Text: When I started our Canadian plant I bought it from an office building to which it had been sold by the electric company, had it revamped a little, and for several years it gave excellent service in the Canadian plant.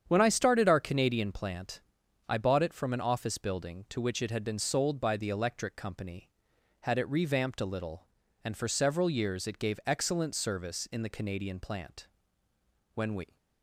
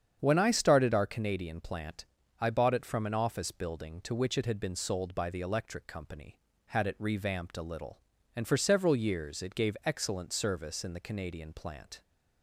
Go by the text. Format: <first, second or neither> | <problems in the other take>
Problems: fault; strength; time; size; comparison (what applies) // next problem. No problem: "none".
second | starts louder than the rest; strong; until 1.0 s; 8.5 dB; strong in the second // pauses between "plant" and "I"; noticeable; at 1.8 s; 0.48 s long; also in the second // goes on to say "When we"; slight; from 12.9 s on; 0.42 s long